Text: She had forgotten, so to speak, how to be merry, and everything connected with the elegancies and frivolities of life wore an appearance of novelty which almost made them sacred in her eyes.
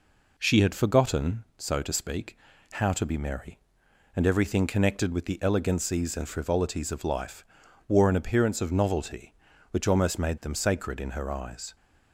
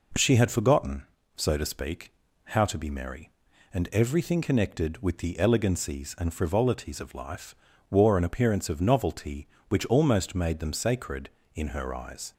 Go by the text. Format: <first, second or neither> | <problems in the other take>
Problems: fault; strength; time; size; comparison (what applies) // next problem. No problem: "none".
neither | pauses between "life" and "wore"; the same in both